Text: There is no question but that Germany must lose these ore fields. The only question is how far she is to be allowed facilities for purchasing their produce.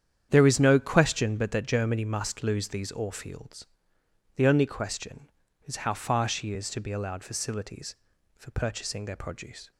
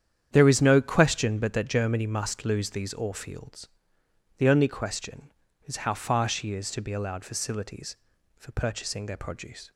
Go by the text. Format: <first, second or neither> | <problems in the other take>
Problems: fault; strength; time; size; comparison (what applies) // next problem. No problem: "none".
neither | starts louder than the rest; strong; the same in both